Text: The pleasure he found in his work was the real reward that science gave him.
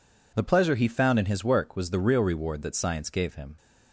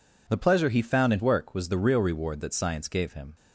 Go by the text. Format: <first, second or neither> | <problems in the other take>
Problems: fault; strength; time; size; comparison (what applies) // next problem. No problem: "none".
first | skips "his"; at 1.1 s